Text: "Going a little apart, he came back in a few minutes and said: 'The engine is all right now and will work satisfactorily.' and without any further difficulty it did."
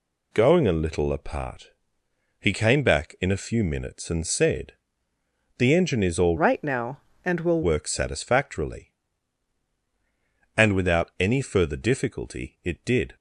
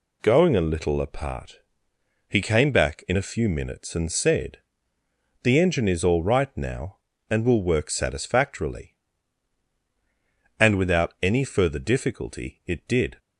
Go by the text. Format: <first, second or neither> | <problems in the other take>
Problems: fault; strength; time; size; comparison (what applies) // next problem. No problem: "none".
second | changes voice from "right" to "will"; from 6.3 to 7.6 s; 1.3 s long